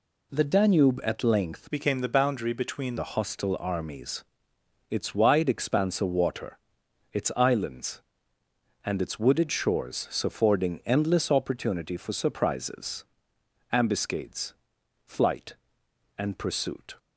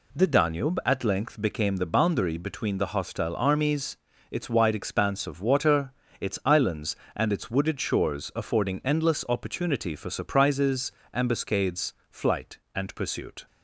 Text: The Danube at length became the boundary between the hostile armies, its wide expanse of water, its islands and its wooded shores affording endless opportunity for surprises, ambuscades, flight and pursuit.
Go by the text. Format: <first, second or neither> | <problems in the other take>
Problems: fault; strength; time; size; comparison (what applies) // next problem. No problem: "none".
second | changes voice from "became" to "between"; from 1.7 to 2.9 s; 1.2 s long // pauses between "shores" and "affording"; slight; at 10.0 s; 0.16 s long